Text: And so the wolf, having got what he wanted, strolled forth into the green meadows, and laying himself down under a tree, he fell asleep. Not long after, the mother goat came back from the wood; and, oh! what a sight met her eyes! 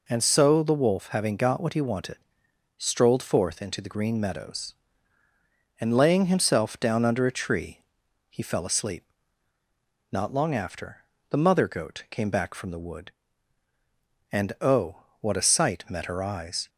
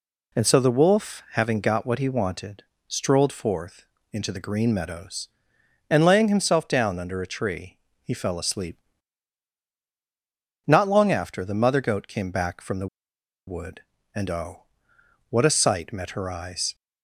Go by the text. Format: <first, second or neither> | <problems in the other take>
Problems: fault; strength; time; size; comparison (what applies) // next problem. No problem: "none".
first | pauses between "forth" and "into"; slight; at 3.8 s; 0.28 s long // pauses between "the" and "wood"; noticeable; at 12.8 s; 0.61 s long